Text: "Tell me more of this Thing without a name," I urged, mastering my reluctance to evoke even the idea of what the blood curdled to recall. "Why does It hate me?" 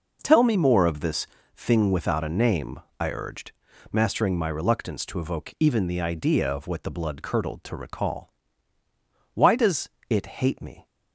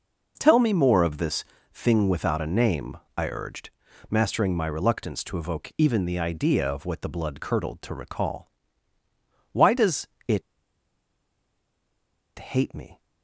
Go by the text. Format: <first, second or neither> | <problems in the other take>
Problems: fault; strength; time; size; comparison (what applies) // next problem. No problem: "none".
first | pauses between "this" and "Thing"; slight; at 1.4 s; 0.28 s long; slight in the first // pauses between "does" and "It"; slight; at 10.0 s; 0.20 s long; slight in the first // pauses between "It" and "hate"; strong; at 10.4 s; 1.9 s long